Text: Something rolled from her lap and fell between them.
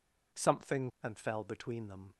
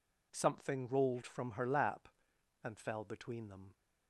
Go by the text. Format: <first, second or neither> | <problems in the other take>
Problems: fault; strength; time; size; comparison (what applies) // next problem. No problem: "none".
second | skips "rolled from her lap"; at 0.9 s